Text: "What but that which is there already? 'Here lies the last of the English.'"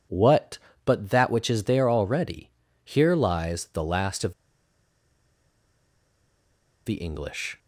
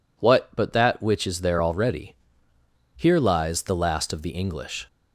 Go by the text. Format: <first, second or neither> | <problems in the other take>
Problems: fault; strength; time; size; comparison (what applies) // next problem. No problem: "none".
second | pauses between "of" and "the"; strong; at 4.3 s; 2.5 s long